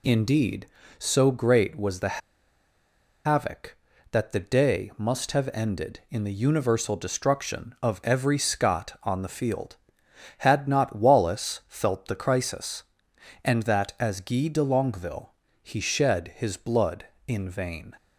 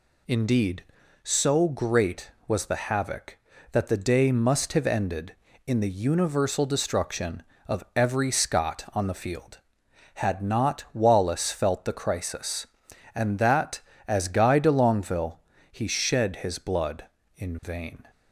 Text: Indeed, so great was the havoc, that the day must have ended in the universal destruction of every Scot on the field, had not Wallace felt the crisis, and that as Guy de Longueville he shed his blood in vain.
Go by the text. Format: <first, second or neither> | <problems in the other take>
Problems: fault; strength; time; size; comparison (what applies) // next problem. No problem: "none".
second | pauses between "the" and "havoc"; at 2.2 s; 1.0 s long // pauses between "Longueville" and "he"; slight; at 15.3 s; 0.32 s long; slight in the second